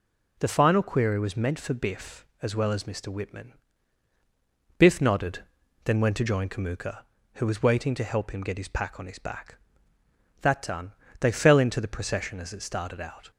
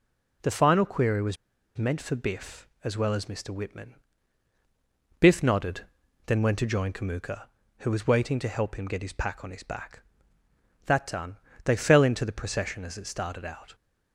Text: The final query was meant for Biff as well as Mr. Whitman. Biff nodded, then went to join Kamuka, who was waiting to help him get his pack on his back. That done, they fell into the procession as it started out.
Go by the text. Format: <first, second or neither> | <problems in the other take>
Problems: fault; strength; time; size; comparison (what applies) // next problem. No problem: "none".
first | pauses between "was" and "meant"; at 1.3 s; 0.40 s long